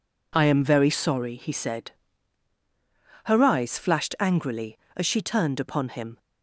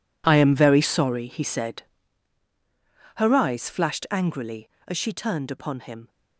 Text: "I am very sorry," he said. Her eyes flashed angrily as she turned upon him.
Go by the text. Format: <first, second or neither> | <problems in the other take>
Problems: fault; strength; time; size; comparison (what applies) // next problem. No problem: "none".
first | gets quieter; strong; throughout; 15 dB